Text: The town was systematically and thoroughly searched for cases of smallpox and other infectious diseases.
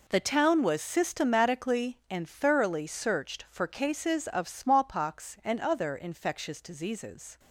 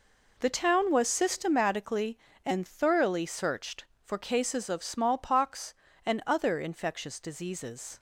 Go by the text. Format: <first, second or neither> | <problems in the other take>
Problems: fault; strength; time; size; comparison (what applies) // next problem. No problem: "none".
second | gets quieter; strong; throughout; 13 dB